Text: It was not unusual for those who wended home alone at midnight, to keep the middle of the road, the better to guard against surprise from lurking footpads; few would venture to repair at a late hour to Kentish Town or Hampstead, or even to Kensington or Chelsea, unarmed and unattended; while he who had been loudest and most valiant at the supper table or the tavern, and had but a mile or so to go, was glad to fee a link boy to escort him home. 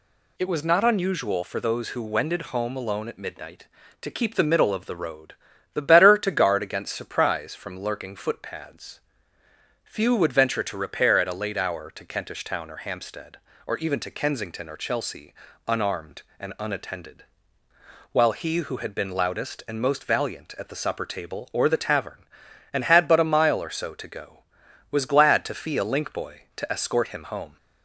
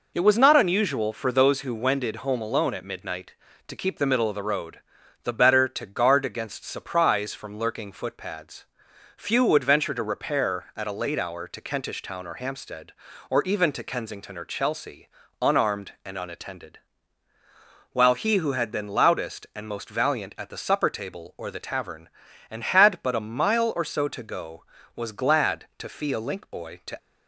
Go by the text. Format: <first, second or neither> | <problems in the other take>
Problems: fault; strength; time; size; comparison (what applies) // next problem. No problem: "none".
first | stops before "escort him home"; at 26.9 s